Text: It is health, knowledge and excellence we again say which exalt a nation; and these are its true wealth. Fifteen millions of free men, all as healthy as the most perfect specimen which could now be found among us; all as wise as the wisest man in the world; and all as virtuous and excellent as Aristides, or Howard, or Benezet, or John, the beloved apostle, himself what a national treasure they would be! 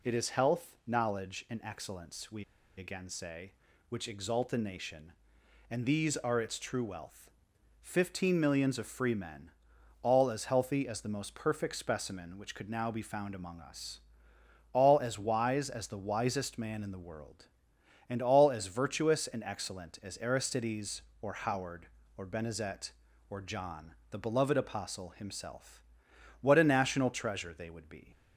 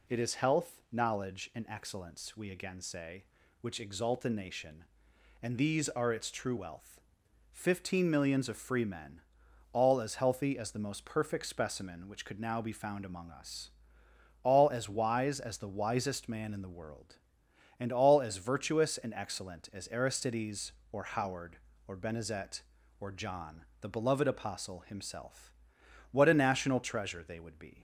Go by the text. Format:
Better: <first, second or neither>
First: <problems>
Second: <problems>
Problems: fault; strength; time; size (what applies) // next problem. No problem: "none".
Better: second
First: pauses between "we" and "again"; slight; at 2.4 s; 0.33 s long // pauses between "himself" and "what"; noticeable; at 25.8 s; 0.60 s long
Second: pauses between "himself" and "what"; noticeable; at 25.5 s; 0.60 s long